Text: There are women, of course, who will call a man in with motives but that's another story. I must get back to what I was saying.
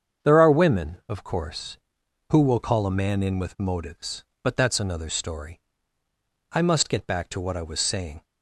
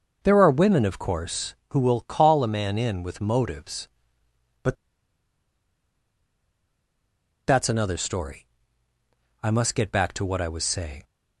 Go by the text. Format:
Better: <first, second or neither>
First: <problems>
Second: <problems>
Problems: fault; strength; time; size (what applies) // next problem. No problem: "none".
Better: first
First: starts louder than the rest; strong; until 1.3 s; 7.5 dB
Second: starts louder than the rest; noticeable; until 1.2 s; 6 dB // pauses between "but" and "that's"; strong; at 4.7 s; 2.7 s long